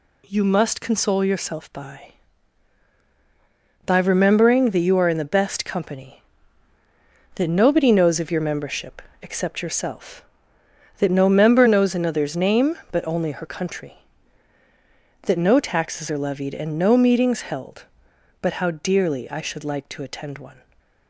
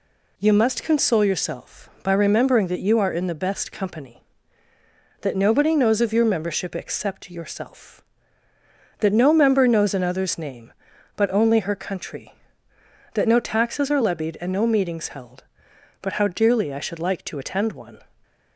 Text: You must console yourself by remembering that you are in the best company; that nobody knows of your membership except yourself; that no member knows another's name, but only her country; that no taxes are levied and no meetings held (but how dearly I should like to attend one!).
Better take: second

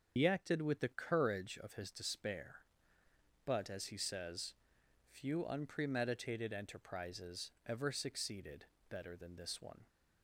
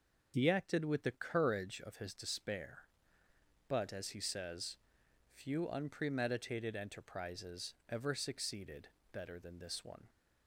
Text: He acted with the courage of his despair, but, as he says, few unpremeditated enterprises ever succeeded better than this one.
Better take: second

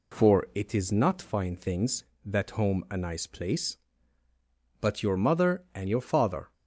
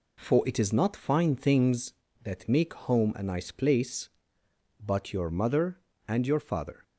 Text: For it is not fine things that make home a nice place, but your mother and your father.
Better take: second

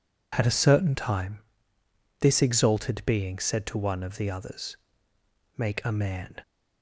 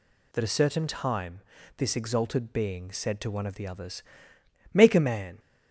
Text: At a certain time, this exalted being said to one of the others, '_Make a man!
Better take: first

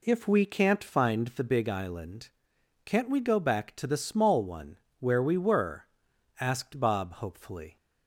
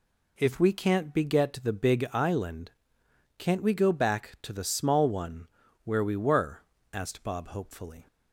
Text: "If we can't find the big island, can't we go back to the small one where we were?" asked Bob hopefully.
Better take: first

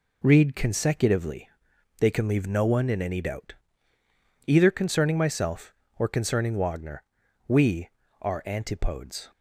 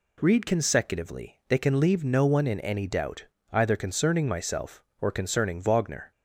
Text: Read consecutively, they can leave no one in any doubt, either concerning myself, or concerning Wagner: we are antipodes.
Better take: first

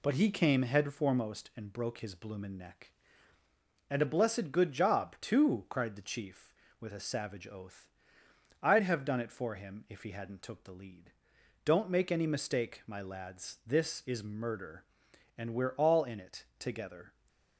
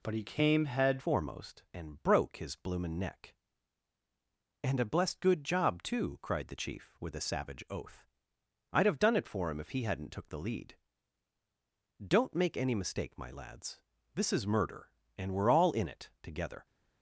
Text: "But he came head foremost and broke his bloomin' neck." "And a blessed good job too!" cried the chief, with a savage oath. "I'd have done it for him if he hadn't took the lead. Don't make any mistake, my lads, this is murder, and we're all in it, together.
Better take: first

